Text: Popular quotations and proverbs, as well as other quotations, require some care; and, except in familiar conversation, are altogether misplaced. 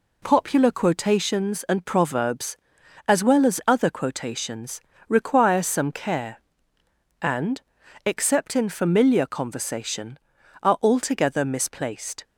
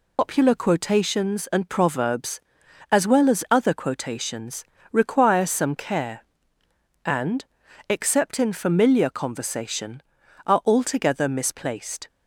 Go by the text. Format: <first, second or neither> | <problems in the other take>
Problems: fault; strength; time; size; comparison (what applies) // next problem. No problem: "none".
first | loses the start of "Popular"; at 0.1 s; 120 ms